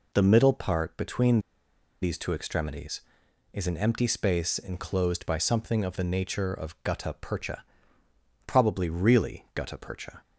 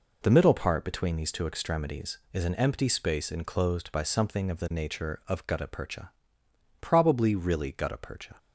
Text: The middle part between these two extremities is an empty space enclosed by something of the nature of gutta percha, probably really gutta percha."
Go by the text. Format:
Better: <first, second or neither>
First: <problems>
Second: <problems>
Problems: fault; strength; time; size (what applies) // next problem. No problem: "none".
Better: second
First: pauses between "between" and "these"; noticeable; at 1.4 s; 0.61 s long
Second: none